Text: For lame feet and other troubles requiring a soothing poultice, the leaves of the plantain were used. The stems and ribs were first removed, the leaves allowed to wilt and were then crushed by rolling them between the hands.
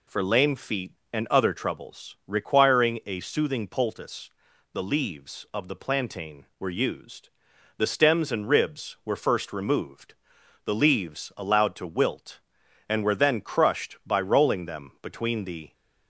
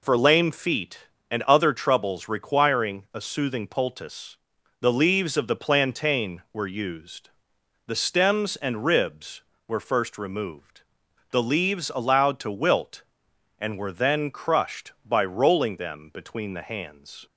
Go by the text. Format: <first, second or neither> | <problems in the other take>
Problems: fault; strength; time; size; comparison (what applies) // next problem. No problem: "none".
second | stops before "hands"; at 15.7 s